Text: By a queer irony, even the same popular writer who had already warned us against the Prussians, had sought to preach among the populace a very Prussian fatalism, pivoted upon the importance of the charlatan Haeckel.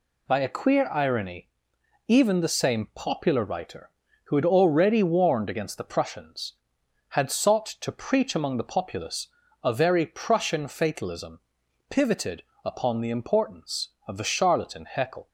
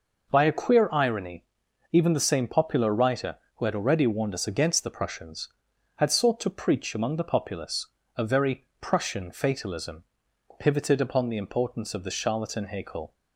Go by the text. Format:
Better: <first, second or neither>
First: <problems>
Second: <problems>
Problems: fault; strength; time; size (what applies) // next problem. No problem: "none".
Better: second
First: skips "us"; at 5.4 s // pauses between "populace" and "a"; slight; at 9.2 s; 0.36 s long // pauses between "pivoted" and "upon"; slight; at 12.4 s; 0.22 s long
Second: pauses between "populace" and "a"; slight; at 7.8 s; 0.30 s long